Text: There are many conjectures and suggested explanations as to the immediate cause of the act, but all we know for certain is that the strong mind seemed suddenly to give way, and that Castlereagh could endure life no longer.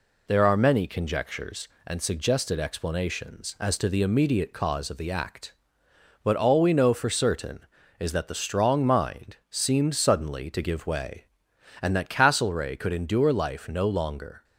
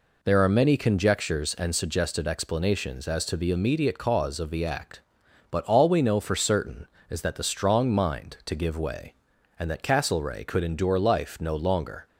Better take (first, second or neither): first